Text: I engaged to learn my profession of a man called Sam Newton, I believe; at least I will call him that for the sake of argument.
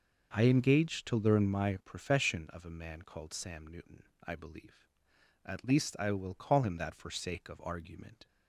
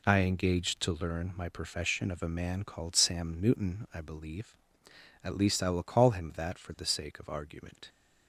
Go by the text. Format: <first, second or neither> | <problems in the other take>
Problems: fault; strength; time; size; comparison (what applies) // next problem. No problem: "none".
second | starts louder than the rest; noticeable; until 1.3 s; 6 dB // skips "the"; at 7.1 s